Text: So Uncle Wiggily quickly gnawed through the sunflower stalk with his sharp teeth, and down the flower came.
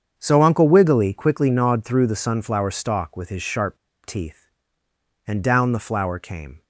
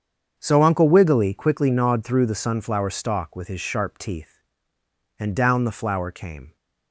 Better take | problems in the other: second | starts louder than the rest; strong; until 1.1 s; 7.5 dB; strong in the second // pauses between "sharp" and "teeth"; slight; at 3.7 s; 0.27 s long

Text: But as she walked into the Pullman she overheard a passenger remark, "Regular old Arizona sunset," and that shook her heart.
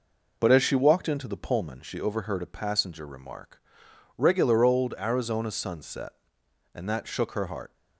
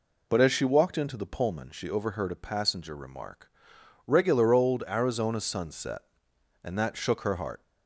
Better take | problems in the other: second | gets quieter; slight; throughout; 3 dB

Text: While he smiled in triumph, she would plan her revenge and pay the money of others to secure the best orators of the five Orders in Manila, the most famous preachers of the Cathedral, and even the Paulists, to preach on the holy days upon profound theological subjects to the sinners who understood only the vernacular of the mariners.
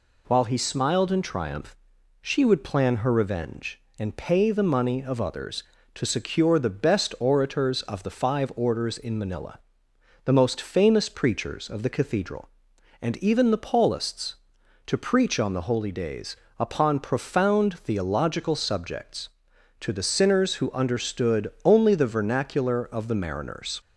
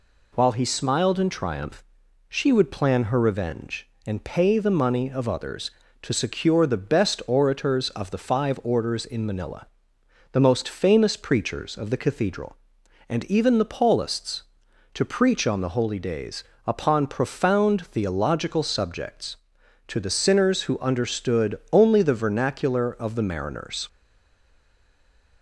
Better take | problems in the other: first | pauses between "days" and "upon"; slight; at 16.4 s; 0.22 s long; slight in the first // stays silent after the last word; noticeable; from 23.8 s on; 1.6 s long

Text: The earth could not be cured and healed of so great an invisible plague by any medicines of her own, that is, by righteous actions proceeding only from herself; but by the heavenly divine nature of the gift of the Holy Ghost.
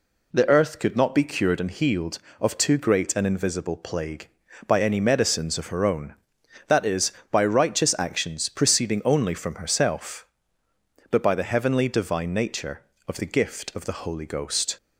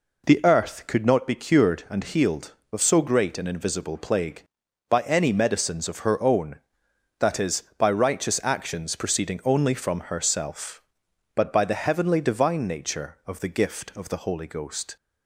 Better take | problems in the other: second | says "too" for "so"; at 2.5 s

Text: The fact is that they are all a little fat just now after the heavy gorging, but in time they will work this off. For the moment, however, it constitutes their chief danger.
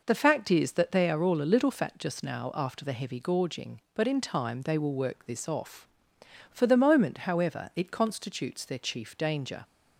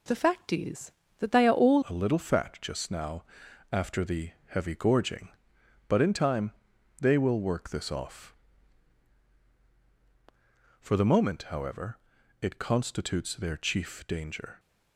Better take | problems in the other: first | changes voice at "a"; from 1.8 s on; 12.7 s long // pauses between "now" and "after"; noticeable; at 3.2 s; 0.48 s long // pauses between "the" and "heavy"; slight; at 4.3 s; 0.16 s long // pauses between "time" and "they"; noticeable; at 6.5 s; 0.46 s long

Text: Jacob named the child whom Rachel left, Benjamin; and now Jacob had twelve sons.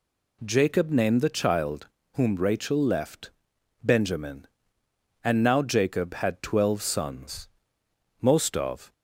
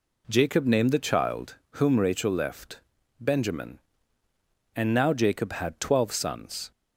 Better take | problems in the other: second | pauses between "child" and "whom"; slight; at 1.8 s; 0.26 s long; slight in the second // goes on to say "Most of"; noticeable; from 8.2 s on; 0.72 s long

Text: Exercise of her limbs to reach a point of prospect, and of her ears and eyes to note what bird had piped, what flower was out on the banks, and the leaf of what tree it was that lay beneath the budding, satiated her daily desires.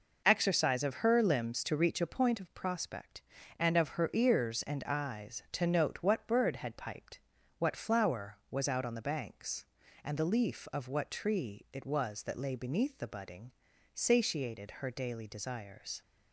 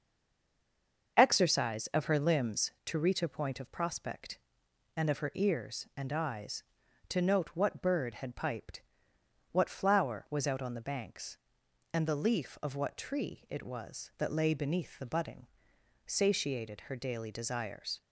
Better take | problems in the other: first | stays silent before the first word; until 1.1 s; 1.1 s long // starts louder than the rest; until 2.2 s; 6.5 dB

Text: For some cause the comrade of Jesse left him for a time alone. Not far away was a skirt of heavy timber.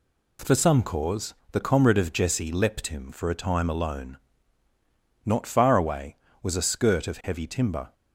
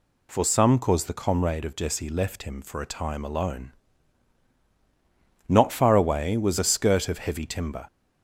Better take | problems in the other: second | pauses between "cause" and "the"; slight; at 1.3 s; 0.18 s long // says "leapt" for "left"; at 2.5 s

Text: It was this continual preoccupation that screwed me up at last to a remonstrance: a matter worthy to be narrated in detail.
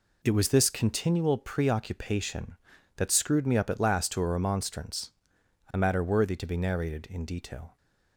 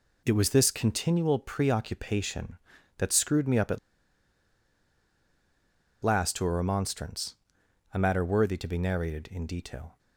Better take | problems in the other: first | pauses between "at" and "last"; strong; at 3.7 s; 2.2 s long

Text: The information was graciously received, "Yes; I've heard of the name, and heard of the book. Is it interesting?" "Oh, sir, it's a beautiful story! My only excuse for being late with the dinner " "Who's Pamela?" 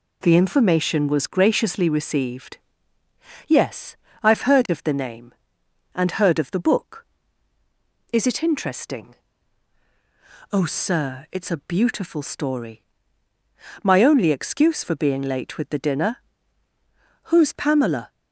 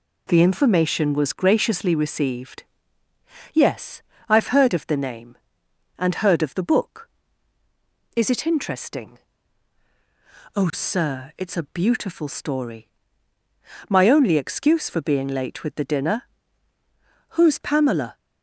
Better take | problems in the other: neither | none

